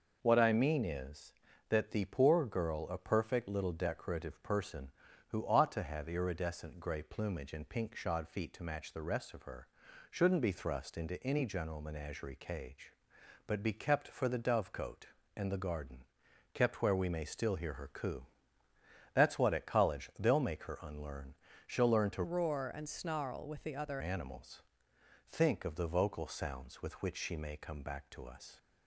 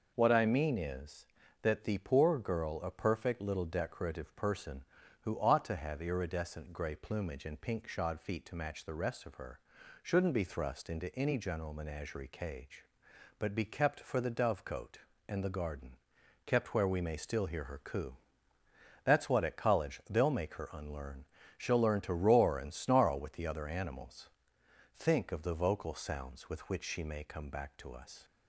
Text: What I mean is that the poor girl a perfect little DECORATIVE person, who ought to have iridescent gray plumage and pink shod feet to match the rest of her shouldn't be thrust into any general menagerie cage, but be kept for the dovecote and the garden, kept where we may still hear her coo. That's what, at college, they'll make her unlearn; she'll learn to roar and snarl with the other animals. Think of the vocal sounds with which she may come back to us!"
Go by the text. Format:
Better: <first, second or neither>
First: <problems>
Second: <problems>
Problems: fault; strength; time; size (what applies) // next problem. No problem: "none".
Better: second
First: pauses between "her" and "shouldn't"; at 9.6 s; 0.44 s long // changes voice from "roar" to "other"; from 22.2 to 24.0 s; 1.8 s long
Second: pauses between "her" and "shouldn't"; at 9.5 s; 0.44 s long